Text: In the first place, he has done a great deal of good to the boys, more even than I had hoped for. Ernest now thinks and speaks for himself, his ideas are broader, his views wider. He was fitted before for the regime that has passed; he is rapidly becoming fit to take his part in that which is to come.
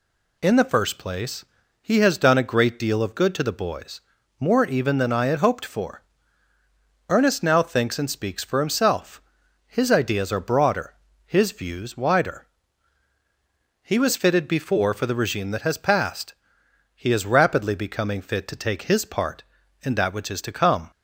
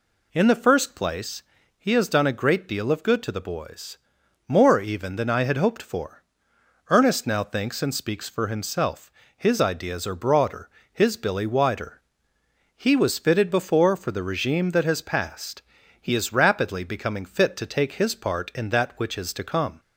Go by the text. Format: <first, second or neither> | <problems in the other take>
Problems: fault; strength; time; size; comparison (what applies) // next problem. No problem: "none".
first | says "billy" for "views"; at 11.1 s